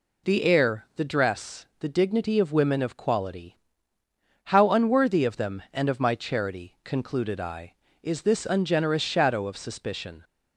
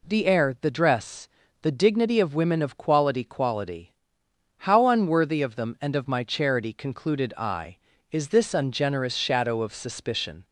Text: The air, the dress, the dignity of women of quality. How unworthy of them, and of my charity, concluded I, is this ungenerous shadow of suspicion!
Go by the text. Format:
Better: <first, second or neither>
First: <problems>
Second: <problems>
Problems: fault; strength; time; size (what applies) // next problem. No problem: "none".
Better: first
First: none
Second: says "quality" twice; at 3.2 s